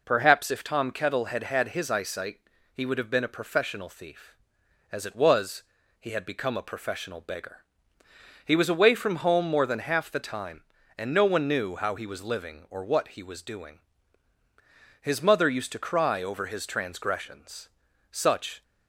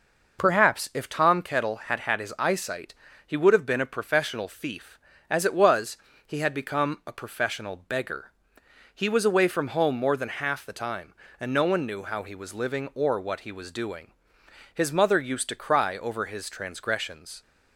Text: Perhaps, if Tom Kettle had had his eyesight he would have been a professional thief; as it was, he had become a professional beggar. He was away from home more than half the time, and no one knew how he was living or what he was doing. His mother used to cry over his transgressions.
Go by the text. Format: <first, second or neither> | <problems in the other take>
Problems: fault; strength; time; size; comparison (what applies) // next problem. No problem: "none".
second | pauses between "eyesight" and "he"; slight; at 2.4 s; 0.34 s long; slight in the second // goes on to say "Such"; from 18.1 s on; 0.52 s long